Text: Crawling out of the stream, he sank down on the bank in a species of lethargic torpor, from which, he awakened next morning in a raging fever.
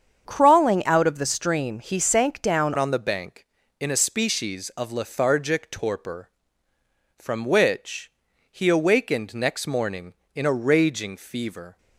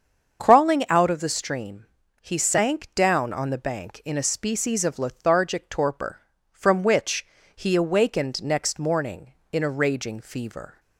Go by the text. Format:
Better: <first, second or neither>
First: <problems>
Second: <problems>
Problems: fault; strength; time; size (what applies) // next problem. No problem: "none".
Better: second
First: starts louder than the rest; strong; until 1.2 s; 7.5 dB // changes voice at "on"; from 2.7 s on; 9.0 s long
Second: starts louder than the rest; until 1.4 s; 7 dB